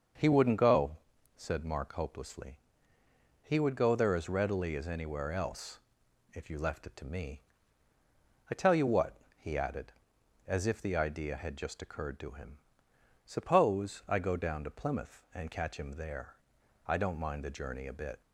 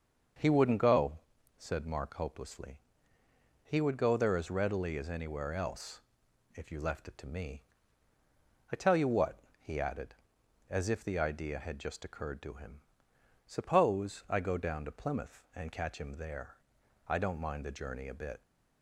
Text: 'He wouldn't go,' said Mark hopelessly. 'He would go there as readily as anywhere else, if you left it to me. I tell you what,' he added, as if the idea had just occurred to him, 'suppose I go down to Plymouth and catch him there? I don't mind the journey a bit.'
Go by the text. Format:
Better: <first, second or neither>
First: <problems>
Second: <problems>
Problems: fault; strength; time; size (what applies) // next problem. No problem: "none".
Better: neither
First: starts louder than the rest; until 1.6 s; 6.5 dB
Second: starts louder than the rest; until 1.7 s; 6.5 dB